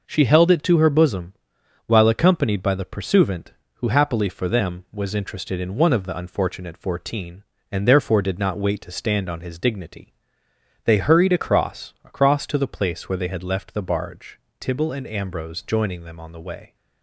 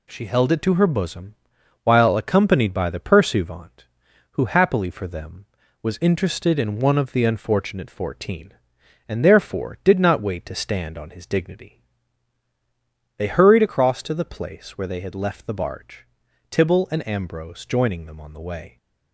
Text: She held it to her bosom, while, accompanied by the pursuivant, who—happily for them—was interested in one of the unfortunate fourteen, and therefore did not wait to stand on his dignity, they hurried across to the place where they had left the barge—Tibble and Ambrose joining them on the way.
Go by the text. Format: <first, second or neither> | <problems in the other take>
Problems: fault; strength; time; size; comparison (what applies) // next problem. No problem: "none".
second | says "across" twice; at 12.0 s